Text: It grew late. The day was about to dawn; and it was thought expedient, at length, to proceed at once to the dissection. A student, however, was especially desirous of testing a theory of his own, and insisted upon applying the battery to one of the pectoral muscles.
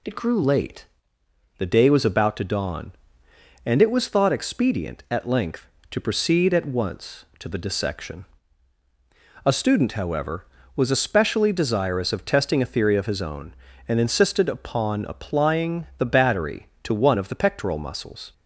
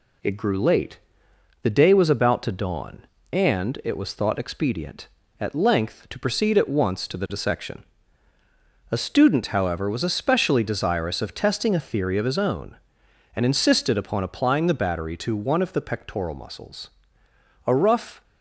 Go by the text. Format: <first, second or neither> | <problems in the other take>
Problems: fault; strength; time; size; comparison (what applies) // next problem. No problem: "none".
first | goes on to say "A rough"; from 17.6 s on; 0.56 s long